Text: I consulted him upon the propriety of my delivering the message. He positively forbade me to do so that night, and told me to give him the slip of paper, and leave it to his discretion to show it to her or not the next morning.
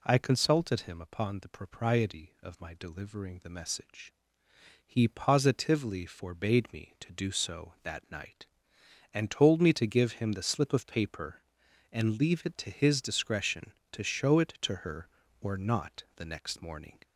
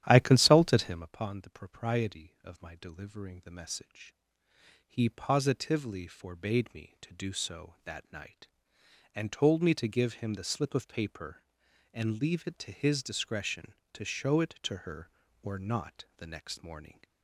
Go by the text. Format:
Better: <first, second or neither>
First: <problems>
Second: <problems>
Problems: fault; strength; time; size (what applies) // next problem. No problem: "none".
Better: first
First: none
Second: starts louder than the rest; strong; until 1.2 s; 11.5 dB